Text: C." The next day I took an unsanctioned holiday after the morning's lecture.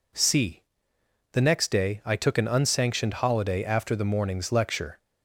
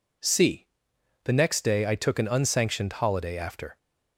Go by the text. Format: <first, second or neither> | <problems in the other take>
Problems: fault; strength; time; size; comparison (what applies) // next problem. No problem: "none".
first | stops before "the morning's lecture"; at 3.7 s